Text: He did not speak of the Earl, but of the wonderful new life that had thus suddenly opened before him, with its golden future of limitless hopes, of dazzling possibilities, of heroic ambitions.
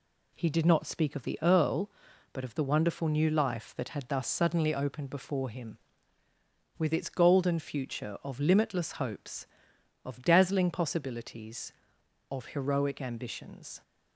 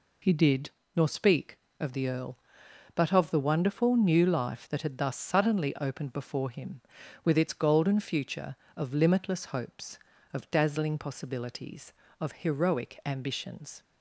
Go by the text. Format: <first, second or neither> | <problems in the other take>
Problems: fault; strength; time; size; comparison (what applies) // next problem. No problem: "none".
first | says "nor" for "not"; at 0.9 s